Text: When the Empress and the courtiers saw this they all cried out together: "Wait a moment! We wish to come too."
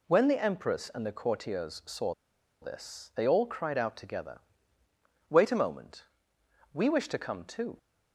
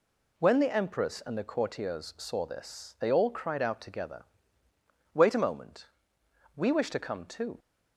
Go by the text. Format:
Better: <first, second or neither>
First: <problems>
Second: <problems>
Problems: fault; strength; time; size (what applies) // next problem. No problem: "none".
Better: second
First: pauses between "saw" and "this"; noticeable; at 2.1 s; 0.49 s long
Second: none